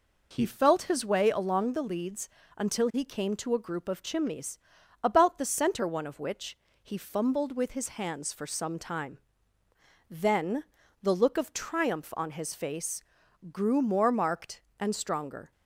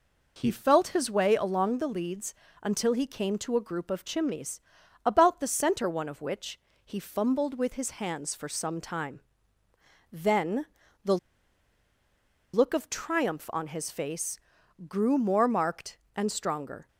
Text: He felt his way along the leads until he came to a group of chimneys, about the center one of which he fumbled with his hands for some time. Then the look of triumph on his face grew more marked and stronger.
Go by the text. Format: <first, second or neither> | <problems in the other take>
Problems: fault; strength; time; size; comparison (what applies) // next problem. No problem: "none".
first | pauses between "leads" and "until"; slight; at 2.3 s; 0.26 s long; slight in the first // pauses between "which" and "he"; slight; at 6.5 s; 0.26 s long; slight in the first // pauses between "Then" and "the"; slight; at 10.6 s; 0.36 s long; slight in the first // pauses between "the" and "look"; strong; at 11.1 s; 1.3 s long // pauses between "face" and "grew"; noticeable; at 14.3 s; 0.52 s long; noticeable in the first